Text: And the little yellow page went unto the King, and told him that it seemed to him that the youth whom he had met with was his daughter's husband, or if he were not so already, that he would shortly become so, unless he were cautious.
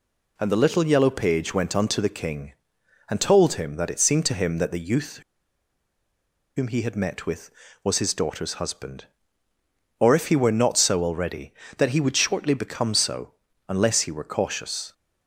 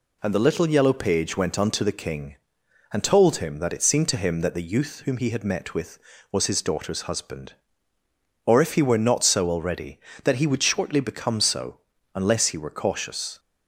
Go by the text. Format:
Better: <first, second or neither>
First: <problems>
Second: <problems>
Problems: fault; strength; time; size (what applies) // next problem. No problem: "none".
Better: second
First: pauses between "youth" and "whom"; strong; at 5.1 s; 1.3 s long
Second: none